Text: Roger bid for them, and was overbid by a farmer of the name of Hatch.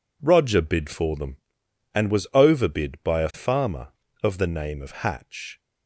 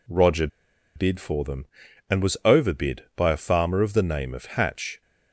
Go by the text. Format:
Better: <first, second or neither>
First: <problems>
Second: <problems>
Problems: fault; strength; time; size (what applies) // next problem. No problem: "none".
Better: first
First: none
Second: pauses between "Roger" and "bid"; noticeable; at 0.4 s; 0.48 s long